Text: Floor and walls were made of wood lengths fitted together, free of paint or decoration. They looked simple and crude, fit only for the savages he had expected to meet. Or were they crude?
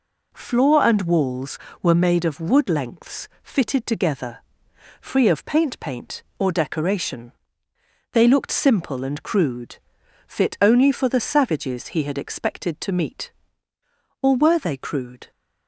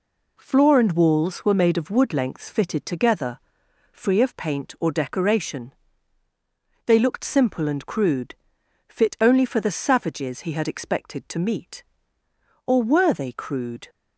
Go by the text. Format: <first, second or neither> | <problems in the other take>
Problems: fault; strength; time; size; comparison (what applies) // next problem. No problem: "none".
second | says "paint" twice; at 5.8 s